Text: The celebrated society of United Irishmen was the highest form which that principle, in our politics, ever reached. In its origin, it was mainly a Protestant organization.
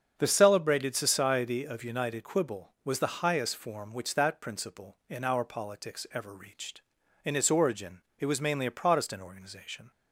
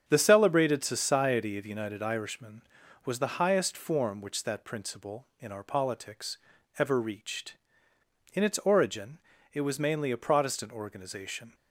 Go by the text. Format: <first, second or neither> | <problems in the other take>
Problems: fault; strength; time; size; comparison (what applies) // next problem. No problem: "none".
second | starts louder than the rest; until 1.1 s; 7 dB; strong in the second // says "Quibble" for "Irishmen"; at 2.2 s